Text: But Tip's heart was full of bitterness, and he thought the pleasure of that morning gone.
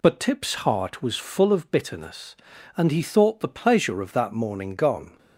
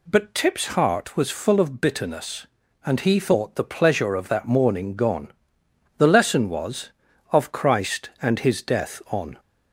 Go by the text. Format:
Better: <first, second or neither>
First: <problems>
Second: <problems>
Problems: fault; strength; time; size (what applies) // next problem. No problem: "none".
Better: first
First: none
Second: goes on to say "The lesson was of Christ and His death on"; strong; from 5.9 s on; 3.4 s long